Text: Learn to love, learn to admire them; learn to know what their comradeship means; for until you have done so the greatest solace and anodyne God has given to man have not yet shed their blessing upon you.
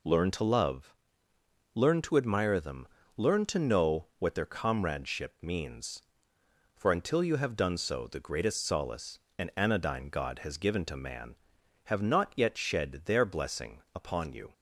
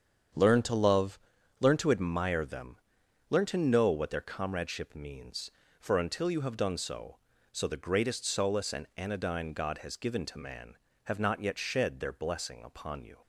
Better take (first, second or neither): first